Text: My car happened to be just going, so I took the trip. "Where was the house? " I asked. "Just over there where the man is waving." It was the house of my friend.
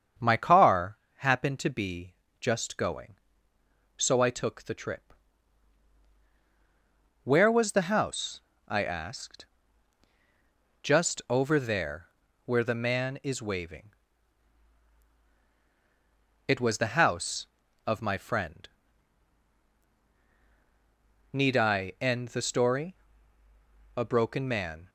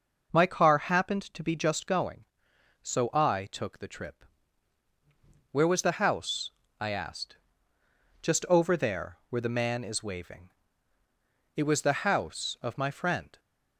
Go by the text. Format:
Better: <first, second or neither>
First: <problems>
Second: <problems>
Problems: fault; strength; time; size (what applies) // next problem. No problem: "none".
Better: second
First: starts louder than the rest; strong; until 1.4 s; 7.5 dB // pauses between "car" and "happened"; slight; at 0.9 s; 0.20 s long // pauses between "be" and "just"; slight; at 2.1 s; 0.24 s long // pauses between "there" and "where"; slight; at 12.0 s; 0.36 s long // goes on to say "Need I end the story A broken man"; strong; from 21.3 s on; 3.5 s long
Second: none